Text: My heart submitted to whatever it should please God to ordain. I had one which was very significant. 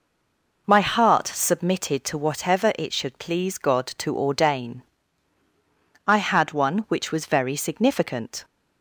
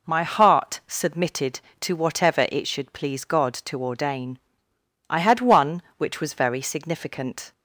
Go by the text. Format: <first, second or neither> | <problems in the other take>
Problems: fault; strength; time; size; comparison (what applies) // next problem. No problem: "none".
second | stays silent before the first word; slight; until 0.6 s; 0.6 s long